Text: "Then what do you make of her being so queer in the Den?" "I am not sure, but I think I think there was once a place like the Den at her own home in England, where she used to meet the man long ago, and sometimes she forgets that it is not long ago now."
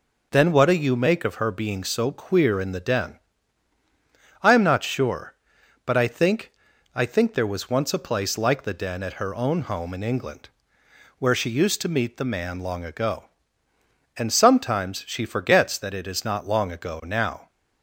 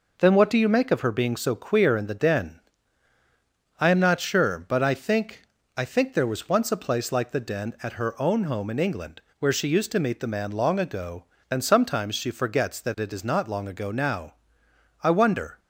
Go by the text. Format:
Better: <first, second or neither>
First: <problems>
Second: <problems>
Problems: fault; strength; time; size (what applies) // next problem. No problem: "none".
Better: first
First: pauses between "think" and "I"; at 6.5 s; 0.42 s long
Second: pauses between "think" and "I"; slight; at 5.4 s; 0.34 s long // goes on to say "I wonder"; from 15.0 s on; 0.54 s long